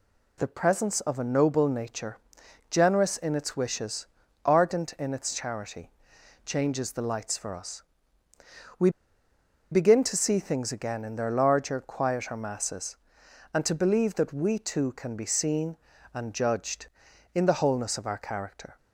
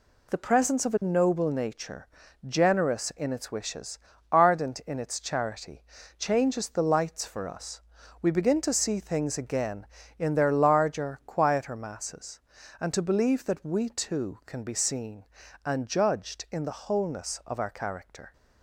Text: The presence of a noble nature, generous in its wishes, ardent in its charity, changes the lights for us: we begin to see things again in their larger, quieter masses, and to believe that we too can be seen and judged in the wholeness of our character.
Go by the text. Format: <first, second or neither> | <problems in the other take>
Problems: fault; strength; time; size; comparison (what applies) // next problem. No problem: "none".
second | pauses between "we" and "begin"; noticeable; at 8.8 s; 0.82 s long